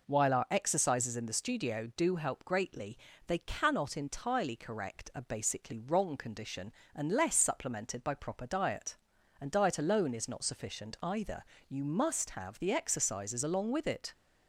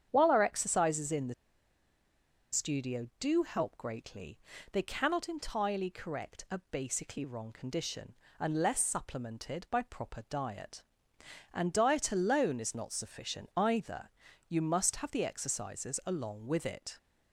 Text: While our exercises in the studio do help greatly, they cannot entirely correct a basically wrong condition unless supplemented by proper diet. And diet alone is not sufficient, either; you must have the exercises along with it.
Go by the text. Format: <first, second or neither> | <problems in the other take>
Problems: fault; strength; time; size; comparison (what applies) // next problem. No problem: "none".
first | starts louder than the rest; strong; until 1.1 s; 8.5 dB // pauses between "the" and "studio"; at 1.3 s; 1.1 s long // pauses between "condition" and "unless"; slight; at 8.1 s; 0.26 s long; slight in the first